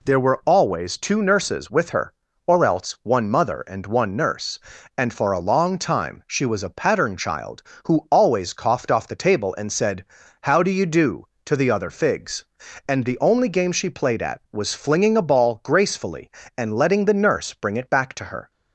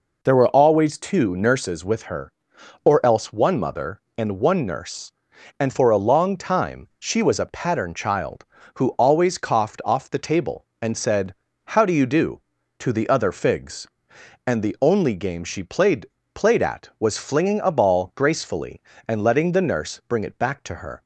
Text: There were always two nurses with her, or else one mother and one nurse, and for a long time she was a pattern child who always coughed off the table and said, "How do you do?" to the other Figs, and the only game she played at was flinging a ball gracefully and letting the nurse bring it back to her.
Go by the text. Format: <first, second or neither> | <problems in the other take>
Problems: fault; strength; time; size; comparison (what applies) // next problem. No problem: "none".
first | says "played" twice; at 16.3 s